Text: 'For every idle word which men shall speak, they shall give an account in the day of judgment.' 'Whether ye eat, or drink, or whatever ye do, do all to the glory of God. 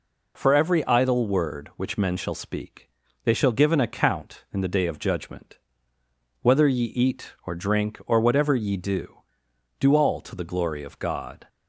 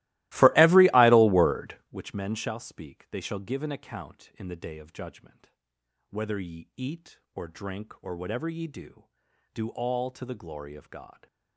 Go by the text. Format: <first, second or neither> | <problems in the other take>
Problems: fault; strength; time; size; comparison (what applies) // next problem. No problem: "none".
first | starts louder than the rest; strong; until 2.0 s; 19 dB